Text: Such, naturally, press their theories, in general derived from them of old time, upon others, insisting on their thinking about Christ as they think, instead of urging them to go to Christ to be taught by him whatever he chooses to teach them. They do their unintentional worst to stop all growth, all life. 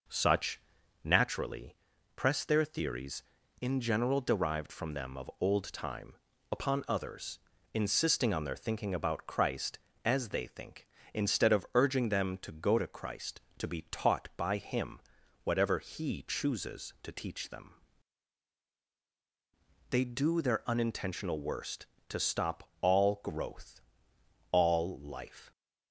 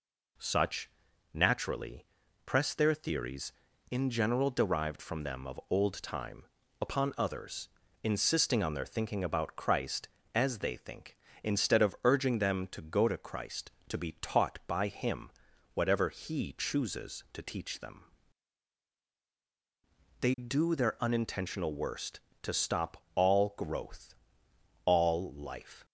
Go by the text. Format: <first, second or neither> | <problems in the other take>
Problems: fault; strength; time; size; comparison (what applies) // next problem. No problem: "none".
second | starts louder than the rest; noticeable; until 1.4 s; 5 dB // pauses between "him" and "whatever"; at 14.9 s; 0.44 s long; also in the second